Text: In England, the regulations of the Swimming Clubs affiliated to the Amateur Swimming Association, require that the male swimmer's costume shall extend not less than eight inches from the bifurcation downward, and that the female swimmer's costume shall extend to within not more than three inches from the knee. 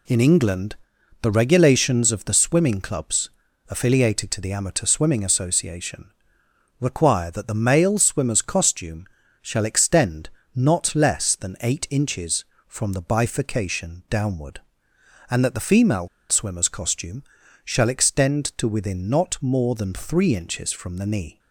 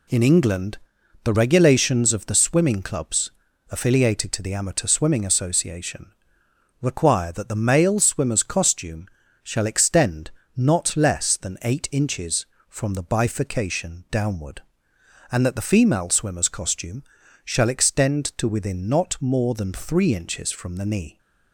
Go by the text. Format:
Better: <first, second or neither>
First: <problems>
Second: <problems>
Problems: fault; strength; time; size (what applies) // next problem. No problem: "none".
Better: second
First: pauses between "Clubs" and "affiliated"; at 3.3 s; 0.38 s long // pauses between "costume" and "shall"; slight; at 9.0 s; 0.34 s long // pauses between "extend" and "not"; slight; at 10.2 s; 0.24 s long // pauses between "female" and "swimmer's"; slight; at 16.0 s; 0.22 s long // pauses between "costume" and "shall"; at 17.2 s; 0.40 s long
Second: pauses between "Clubs" and "affiliated"; at 3.3 s; 0.38 s long // pauses between "costume" and "shall"; slight; at 9.0 s; 0.34 s long // pauses between "extend" and "not"; slight; at 10.3 s; 0.24 s long // pauses between "costume" and "shall"; at 17.0 s; 0.40 s long